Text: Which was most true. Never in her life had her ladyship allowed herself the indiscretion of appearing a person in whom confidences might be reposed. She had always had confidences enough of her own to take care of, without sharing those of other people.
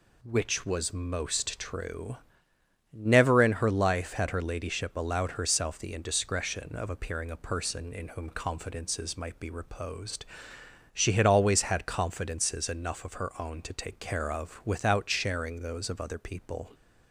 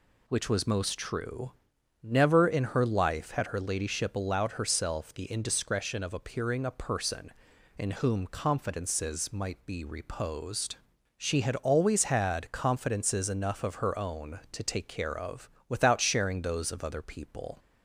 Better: neither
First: none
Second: none

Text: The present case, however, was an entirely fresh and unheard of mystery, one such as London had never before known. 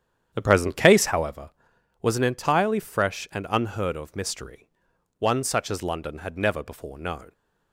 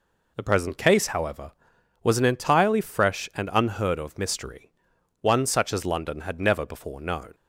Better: second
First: starts louder than the rest; strong; until 1.4 s; 9 dB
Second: none

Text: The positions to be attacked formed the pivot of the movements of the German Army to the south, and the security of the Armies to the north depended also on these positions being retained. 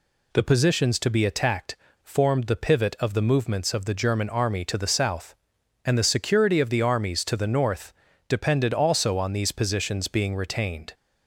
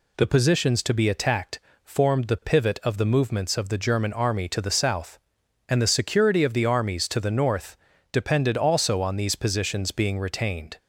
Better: neither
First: pauses between "attacked" and "formed"; slight; at 1.7 s; 0.26 s long // pauses between "north" and "depended"; slight; at 7.9 s; 0.34 s long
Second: pauses between "attacked" and "formed"; slight; at 1.5 s; 0.24 s long // pauses between "north" and "depended"; slight; at 7.7 s; 0.34 s long

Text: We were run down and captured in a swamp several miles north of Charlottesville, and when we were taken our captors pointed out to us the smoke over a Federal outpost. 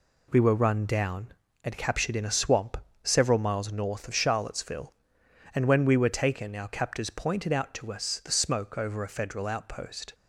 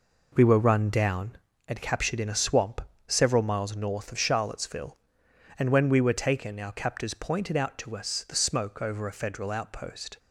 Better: first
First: pauses between "swamp" and "several"; slight; at 2.7 s; 0.26 s long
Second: starts louder than the rest; noticeable; until 1.6 s; 4.5 dB // pauses between "swamp" and "several"; slight; at 2.8 s; 0.26 s long

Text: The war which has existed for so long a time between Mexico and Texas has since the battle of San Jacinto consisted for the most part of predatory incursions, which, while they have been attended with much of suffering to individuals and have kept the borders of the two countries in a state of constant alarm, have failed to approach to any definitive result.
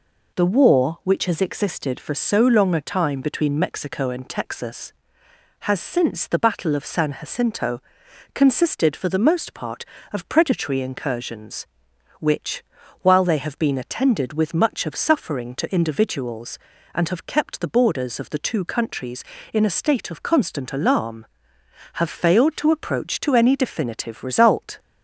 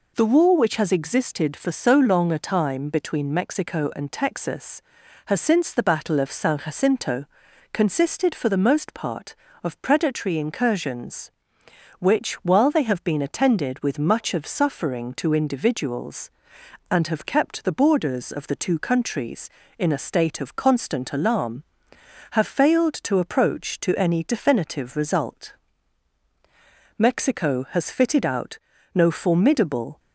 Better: first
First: pauses between "Jacinto" and "consisted"; noticeable; at 7.8 s; 0.50 s long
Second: pauses between "Jacinto" and "consisted"; noticeable; at 7.2 s; 0.46 s long // goes on to say "Mexico has fitted out no formidable"; strong; from 26.9 s on; 3.0 s long

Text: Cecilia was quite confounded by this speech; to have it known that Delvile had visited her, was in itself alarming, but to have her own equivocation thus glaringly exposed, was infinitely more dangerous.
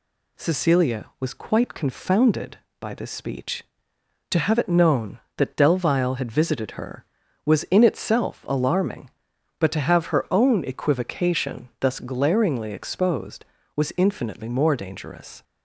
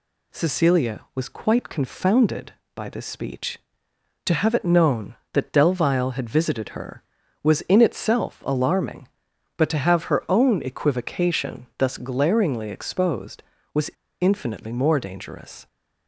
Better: first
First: none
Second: pauses between "was" and "infinitely"; slight; at 13.9 s; 0.29 s long

